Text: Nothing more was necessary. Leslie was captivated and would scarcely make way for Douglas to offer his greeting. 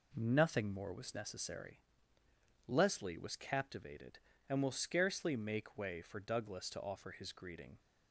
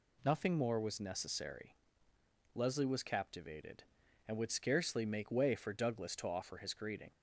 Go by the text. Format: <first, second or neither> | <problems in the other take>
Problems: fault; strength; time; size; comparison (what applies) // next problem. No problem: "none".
second | says "will" for "would"; at 4.6 s